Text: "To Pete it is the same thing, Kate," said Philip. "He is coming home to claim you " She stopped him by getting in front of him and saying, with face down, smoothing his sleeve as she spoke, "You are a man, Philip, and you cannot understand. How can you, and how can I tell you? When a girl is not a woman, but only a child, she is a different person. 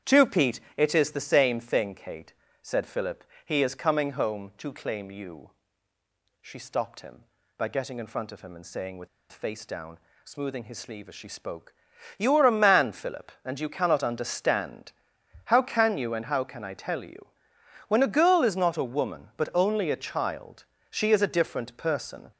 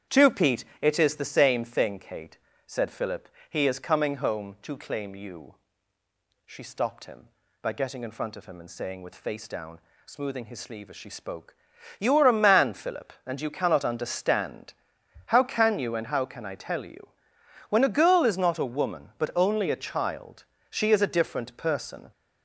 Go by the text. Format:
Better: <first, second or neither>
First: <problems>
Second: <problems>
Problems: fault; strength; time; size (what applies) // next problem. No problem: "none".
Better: second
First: starts louder than the rest; strong; until 1.2 s; 9 dB // pauses between "Pete" and "it"; slight; at 0.5 s; 0.16 s long // pauses between "with" and "face"; slight; at 9.0 s; 0.23 s long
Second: starts louder than the rest; strong; until 1.2 s; 9 dB // pauses between "Pete" and "it"; slight; at 0.6 s; 0.16 s long